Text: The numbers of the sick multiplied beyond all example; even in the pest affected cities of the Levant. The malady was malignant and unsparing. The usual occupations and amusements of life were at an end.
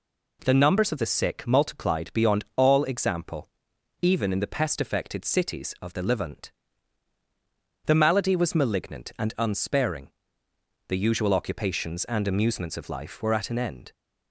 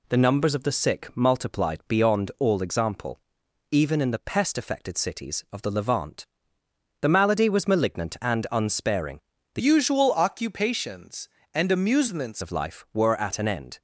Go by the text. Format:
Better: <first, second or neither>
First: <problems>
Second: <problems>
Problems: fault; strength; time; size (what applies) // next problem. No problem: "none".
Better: first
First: none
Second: changes voice from "usual" to "amusements"; from 9.5 to 12.4 s; 2.9 s long